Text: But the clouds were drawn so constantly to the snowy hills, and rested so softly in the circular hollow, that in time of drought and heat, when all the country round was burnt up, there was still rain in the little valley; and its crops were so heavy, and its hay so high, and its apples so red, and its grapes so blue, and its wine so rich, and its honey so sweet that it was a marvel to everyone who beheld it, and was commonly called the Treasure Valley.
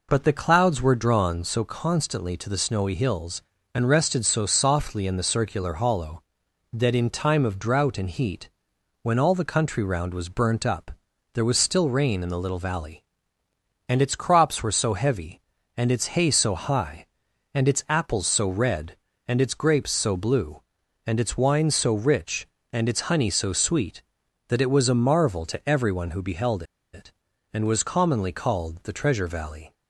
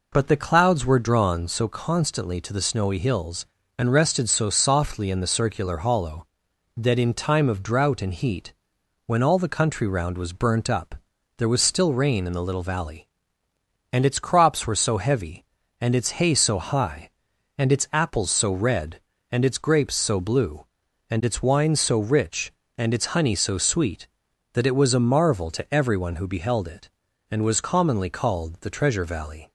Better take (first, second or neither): second